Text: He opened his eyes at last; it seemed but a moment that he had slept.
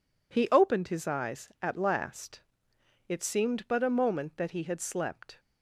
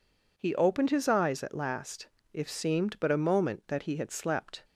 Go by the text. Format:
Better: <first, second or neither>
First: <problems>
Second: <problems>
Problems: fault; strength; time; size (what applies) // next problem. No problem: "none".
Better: first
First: none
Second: says "if" for "it"; at 2.3 s